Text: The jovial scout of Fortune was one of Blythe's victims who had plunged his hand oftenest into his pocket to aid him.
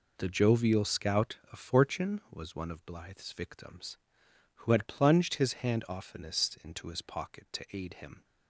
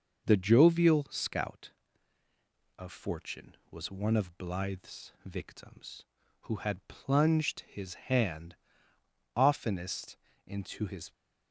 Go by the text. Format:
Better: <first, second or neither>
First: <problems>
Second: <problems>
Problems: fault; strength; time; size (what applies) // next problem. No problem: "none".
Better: first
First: none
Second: pauses between "hand" and "oftenest"; noticeable; at 8.5 s; 0.80 s long // pauses between "oftenest" and "into"; slight; at 10.1 s; 0.30 s long // stops before "pocket to aid him"; at 11.1 s